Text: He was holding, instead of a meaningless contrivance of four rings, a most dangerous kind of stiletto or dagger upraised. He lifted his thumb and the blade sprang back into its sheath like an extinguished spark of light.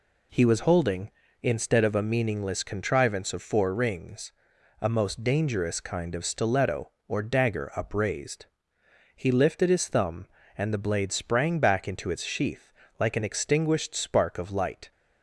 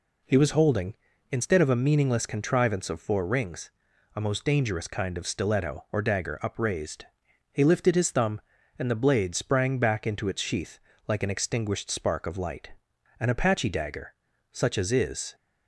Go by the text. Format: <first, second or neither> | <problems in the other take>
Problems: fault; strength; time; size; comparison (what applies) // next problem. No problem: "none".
first | pauses between "sheath" and "like"; slight; at 10.7 s; 0.28 s long; slight in the first // goes on to say "An Apache dagger such as is"; strong; from 13.1 s on; 2.1 s long